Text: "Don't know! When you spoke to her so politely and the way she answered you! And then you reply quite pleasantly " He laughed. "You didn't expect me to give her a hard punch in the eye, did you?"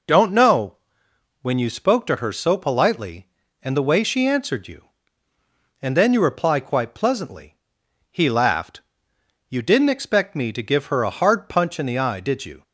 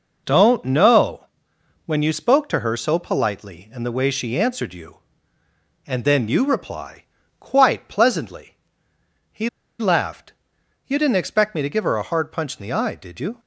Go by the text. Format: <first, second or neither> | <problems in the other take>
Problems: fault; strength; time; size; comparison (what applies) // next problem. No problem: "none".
first | pauses between "reply" and "quite"; slight; at 7.0 s; 0.36 s long // pauses between "He" and "laughed"; slight; at 9.4 s; 0.30 s long